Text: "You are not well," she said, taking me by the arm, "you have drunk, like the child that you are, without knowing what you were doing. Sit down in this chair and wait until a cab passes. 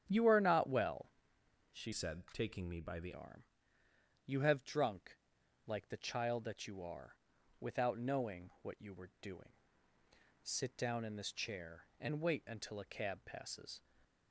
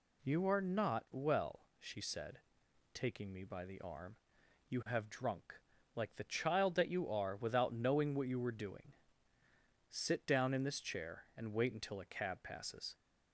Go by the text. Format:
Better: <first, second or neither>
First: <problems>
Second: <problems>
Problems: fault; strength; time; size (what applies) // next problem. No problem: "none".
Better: second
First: starts louder than the rest; strong; until 1.1 s; 9 dB // changes voice from "said" to "the"; from 1.9 to 3.1 s; 1.2 s long // stays silent after the last word; slight; from 13.7 s on; 0.6 s long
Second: none